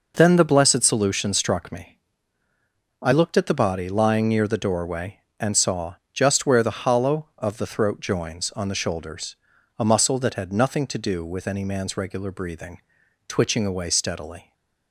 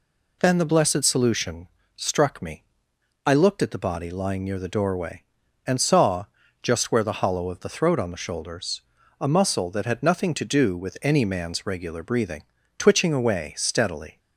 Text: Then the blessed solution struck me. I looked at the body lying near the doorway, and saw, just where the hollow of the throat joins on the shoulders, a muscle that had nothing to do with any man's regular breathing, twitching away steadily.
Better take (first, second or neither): first